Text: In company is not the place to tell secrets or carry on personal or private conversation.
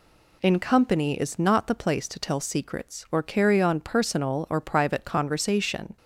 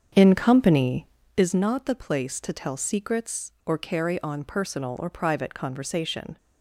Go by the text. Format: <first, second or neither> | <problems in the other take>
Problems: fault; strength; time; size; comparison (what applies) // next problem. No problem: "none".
first | starts louder than the rest; strong; until 1.5 s; 7.5 dB